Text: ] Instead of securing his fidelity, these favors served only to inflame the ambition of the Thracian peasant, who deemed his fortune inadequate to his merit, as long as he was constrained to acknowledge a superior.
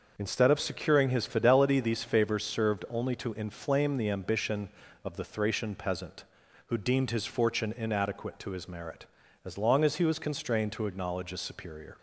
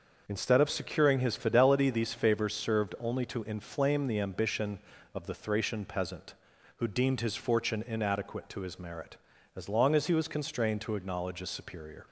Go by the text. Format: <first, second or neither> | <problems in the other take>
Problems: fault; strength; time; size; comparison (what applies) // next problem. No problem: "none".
neither | starts louder than the rest; noticeable; the same in both